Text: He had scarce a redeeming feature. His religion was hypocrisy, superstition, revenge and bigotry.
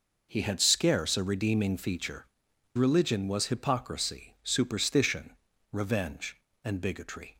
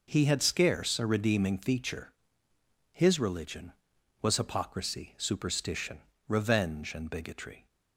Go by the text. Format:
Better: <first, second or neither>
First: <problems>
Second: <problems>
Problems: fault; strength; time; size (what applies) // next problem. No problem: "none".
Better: second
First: skips "His"; at 2.5 s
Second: none